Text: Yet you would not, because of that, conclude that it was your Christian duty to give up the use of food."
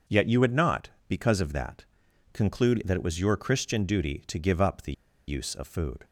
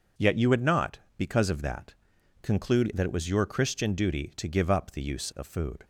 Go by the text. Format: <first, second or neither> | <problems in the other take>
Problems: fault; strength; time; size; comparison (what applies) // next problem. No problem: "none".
second | pauses between "the" and "use"; slight; at 4.9 s; 0.34 s long